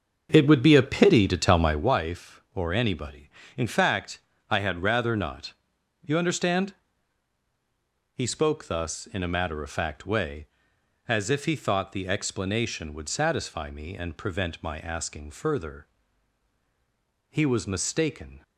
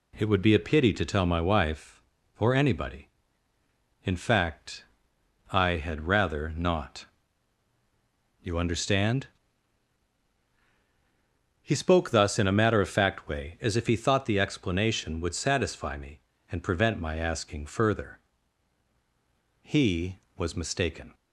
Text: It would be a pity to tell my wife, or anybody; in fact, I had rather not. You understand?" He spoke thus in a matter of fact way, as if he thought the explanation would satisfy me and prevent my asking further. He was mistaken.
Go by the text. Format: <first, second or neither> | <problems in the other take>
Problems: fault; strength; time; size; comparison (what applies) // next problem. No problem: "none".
second | starts louder than the rest; until 2.0 s; 6.5 dB